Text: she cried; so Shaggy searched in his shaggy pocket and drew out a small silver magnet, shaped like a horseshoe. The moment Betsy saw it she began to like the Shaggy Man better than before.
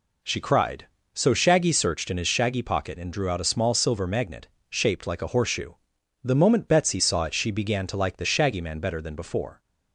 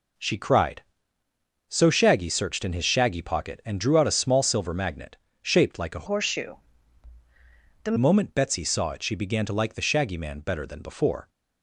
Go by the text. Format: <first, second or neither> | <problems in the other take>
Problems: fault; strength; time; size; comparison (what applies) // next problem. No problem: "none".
first | changes voice from "horseshoe" to "The"; from 6.0 to 7.9 s; 1.9 s long